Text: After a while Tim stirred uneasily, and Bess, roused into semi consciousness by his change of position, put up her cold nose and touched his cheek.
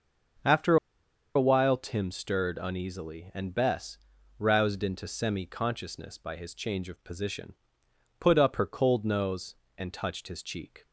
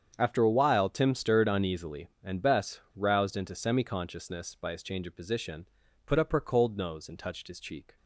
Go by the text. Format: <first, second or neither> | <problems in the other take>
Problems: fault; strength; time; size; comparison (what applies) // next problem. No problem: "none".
second | starts louder than the rest; until 2.0 s; 6.5 dB; strong in the second // pauses between "After" and "a"; noticeable; at 0.7 s; 0.59 s long